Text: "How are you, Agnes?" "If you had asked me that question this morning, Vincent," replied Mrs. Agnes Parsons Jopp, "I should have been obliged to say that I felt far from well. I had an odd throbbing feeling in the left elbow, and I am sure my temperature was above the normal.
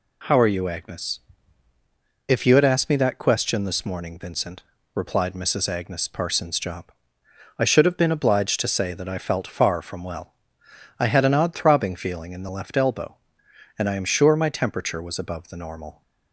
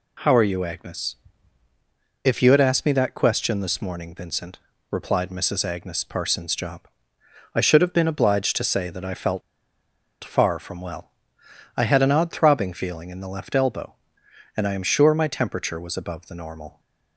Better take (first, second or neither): first